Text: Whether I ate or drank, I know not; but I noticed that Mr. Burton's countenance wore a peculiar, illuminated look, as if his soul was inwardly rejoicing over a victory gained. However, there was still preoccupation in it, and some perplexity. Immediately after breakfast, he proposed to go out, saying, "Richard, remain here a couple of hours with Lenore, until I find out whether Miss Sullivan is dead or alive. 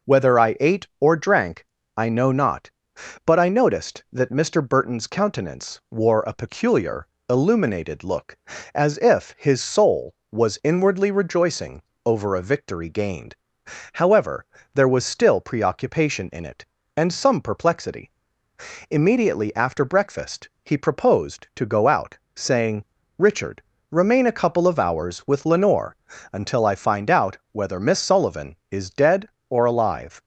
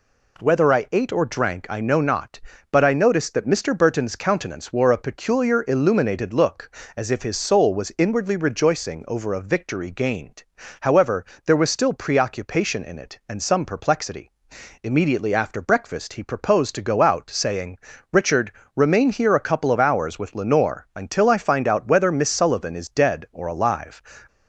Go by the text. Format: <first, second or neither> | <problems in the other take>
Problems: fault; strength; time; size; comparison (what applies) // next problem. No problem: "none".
second | pauses between "rejoicing" and "over"; slight; at 11.7 s; 0.24 s long // skips "here"; at 24.2 s